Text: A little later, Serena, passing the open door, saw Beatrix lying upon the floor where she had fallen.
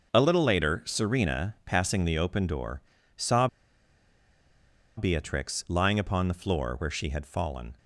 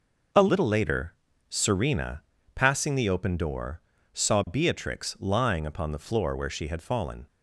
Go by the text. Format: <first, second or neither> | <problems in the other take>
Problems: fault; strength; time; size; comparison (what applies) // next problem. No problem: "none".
second | starts louder than the rest; noticeable; until 1.1 s; 6 dB // pauses between "saw" and "Beatrix"; strong; at 3.4 s; 1.5 s long